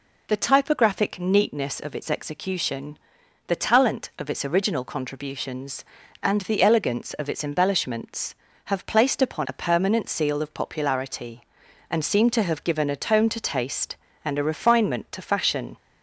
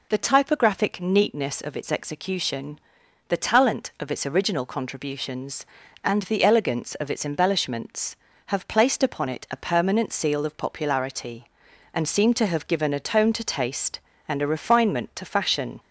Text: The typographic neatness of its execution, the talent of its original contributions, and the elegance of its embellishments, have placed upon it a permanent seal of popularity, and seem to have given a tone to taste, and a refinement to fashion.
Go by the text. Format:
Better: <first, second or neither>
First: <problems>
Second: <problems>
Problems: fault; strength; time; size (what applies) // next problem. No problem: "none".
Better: second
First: skips "it"; at 9.4 s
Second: none